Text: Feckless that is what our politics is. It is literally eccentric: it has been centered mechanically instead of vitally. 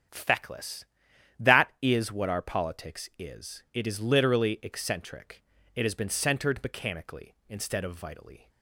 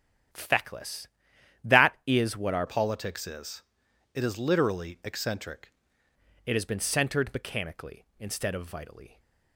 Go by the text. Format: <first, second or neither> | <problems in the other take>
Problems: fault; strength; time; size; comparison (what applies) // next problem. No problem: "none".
first | starts louder than the rest; strong; until 1.9 s; 10 dB; strong in the first // changes voice from "politics" to "eccentric"; from 2.6 to 5.7 s; 3.1 s long